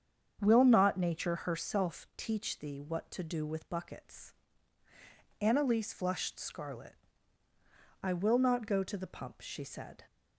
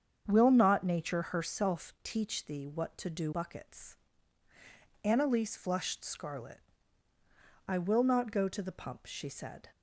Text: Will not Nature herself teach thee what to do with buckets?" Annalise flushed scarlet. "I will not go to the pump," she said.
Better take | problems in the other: first | starts louder than the rest; strong; until 1.2 s; 7.5 dB; strong in the first // skips "with"; at 3.3 s

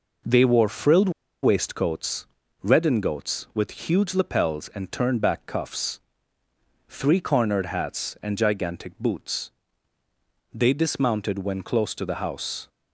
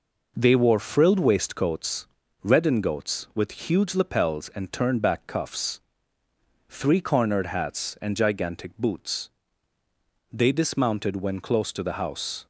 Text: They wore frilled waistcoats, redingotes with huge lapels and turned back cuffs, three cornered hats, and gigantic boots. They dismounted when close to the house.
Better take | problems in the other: second | pauses between "frilled" and "waistcoats"; slight; at 1.1 s; 0.32 s long

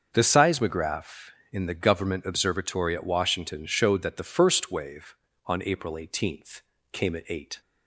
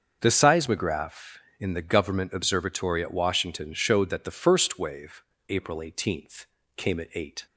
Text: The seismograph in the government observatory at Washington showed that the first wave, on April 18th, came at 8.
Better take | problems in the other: first | starts louder than the rest; until 1.2 s; 6.5 dB; also in the first // skips "on"; at 5.3 s

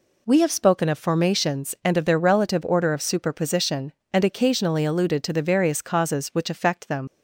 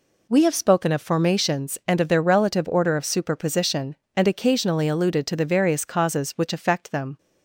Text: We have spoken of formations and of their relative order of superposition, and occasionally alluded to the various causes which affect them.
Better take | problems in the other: second | leaves "them" unfinished; at 7.0 s; 70 ms

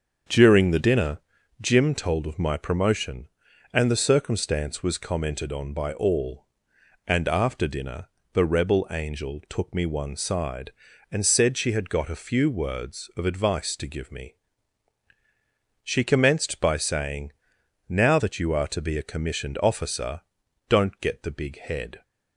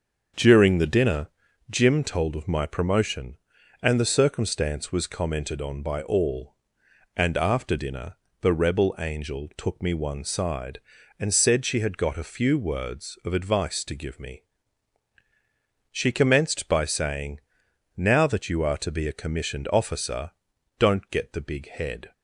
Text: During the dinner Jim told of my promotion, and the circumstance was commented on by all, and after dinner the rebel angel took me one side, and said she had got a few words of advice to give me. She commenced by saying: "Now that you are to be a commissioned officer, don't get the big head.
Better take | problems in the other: neither | starts louder than the rest; the same in both // pauses between "dinner" and "Jim"; the same in both // pauses between "dinner" and "the"; slight; the same in both

